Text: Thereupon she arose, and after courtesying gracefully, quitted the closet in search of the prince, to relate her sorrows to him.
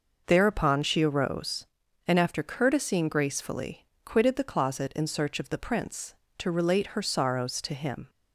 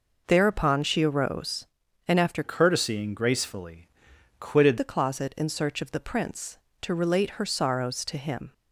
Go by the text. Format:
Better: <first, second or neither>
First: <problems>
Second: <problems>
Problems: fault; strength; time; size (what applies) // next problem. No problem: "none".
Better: first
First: none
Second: changes voice from "courtesying" to "quitted"; from 2.4 to 4.7 s; 2.3 s long